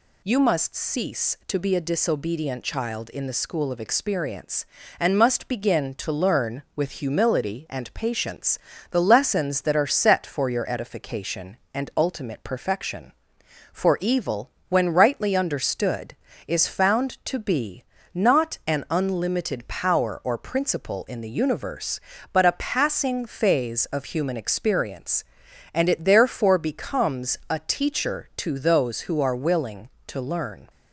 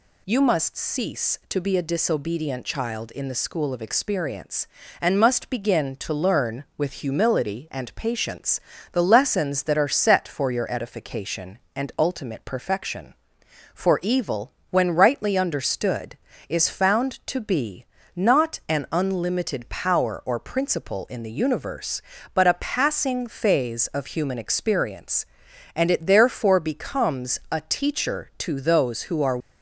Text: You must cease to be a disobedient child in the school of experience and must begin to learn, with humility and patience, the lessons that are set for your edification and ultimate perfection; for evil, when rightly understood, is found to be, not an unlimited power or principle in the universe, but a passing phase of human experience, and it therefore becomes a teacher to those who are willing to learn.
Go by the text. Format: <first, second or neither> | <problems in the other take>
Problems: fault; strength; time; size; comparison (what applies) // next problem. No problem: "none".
first | stops before "willing to learn"; at 29.3 s